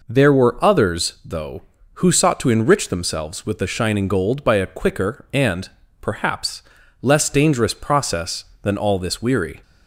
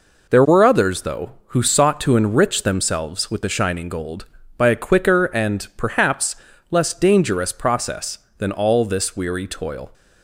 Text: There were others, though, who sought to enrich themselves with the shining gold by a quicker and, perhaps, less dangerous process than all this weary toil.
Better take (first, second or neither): second